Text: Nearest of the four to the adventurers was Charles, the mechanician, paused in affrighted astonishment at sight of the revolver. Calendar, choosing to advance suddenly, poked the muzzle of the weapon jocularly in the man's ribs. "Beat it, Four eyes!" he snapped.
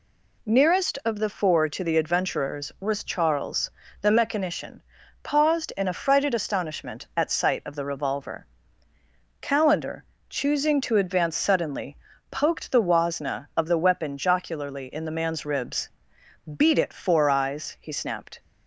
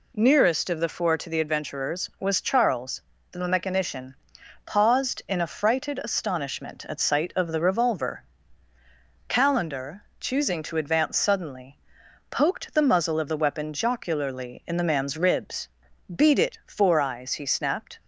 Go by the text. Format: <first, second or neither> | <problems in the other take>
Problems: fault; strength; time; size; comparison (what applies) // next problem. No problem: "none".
second | says "wasna" for "muzzle"; at 12.8 s